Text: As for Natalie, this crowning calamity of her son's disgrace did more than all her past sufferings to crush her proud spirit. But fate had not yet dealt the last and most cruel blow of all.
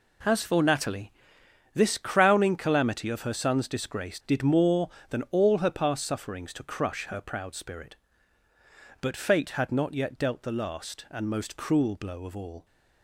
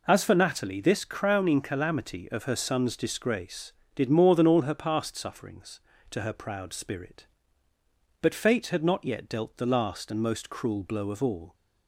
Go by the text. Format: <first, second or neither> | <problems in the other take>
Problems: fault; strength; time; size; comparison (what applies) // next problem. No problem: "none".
first | skips "crush"; at 6.2 s